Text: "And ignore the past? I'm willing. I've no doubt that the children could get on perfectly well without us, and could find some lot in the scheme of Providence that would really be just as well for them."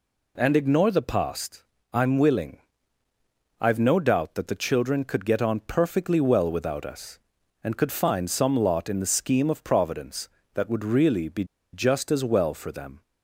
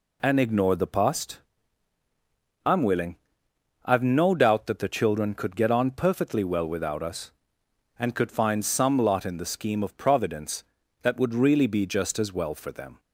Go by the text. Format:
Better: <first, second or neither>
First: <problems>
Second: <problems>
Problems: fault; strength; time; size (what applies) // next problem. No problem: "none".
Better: second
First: pauses between "be" and "just"; slight; at 11.4 s; 0.28 s long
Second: none